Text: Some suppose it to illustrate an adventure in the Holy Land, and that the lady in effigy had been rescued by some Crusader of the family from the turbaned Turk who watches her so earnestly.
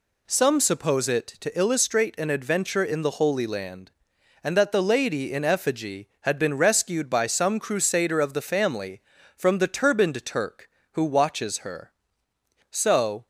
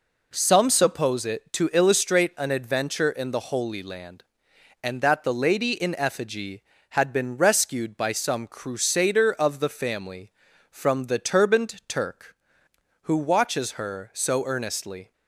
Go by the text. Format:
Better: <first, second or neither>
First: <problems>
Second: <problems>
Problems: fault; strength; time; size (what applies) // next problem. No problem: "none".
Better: second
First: stops before "earnestly"; at 13.2 s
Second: none